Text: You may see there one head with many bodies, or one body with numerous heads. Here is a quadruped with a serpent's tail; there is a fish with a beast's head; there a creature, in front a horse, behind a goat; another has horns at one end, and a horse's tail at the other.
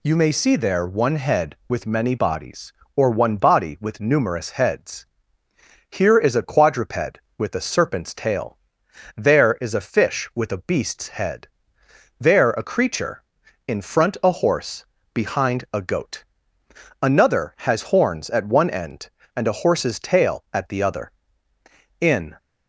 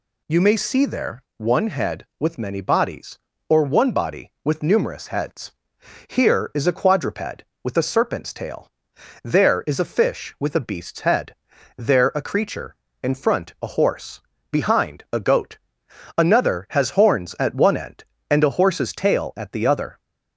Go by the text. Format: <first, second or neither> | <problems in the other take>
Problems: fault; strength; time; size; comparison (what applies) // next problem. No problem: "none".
second | goes on to say "In"; slight; from 21.9 s on; 0.38 s long